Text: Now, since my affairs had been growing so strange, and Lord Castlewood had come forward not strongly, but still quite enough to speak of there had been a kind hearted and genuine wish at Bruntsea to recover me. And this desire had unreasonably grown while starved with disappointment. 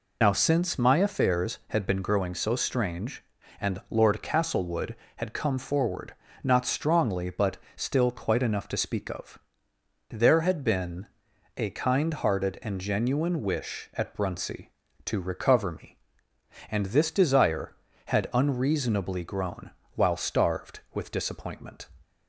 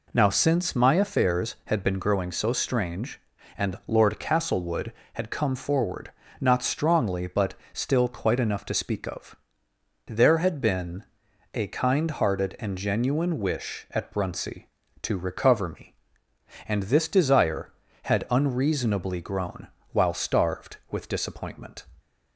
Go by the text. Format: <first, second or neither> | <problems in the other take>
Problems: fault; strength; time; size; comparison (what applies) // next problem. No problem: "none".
second | loses the start of "Now"; at 0.2 s; 100 ms // pauses between "forward" and "not"; slight; at 6.1 s; 0.30 s long; slight in the second // pauses between "but" and "still"; slight; at 7.5 s; 0.20 s long; slight in the second // pauses between "of" and "there"; noticeable; at 9.3 s; 0.72 s long; noticeable in the second // pauses between "been" and "a"; noticeable; at 11.0 s; 0.50 s long; noticeable in the second // pauses between "grown" and "while"; slight; at 19.6 s; 0.26 s long; slight in the second